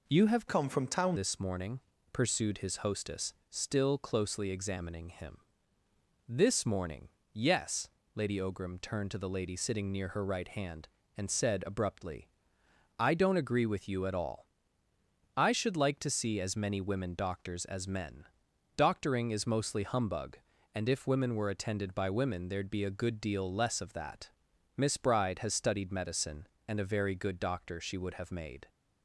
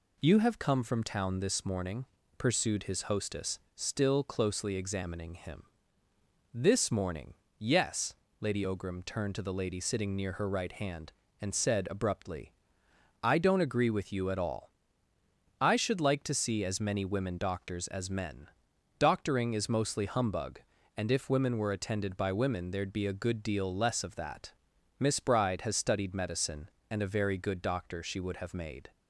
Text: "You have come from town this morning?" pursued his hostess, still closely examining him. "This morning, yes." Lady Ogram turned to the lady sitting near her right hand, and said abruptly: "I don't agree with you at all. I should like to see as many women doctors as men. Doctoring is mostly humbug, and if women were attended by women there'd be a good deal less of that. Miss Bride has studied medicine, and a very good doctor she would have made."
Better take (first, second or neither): second